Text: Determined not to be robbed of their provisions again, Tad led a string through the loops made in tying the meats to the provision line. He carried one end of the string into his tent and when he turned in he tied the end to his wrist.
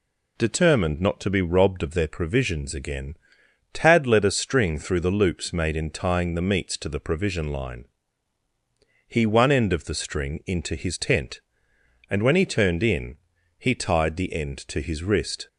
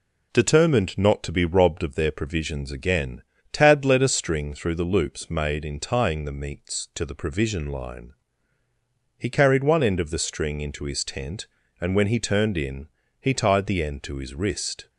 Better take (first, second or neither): second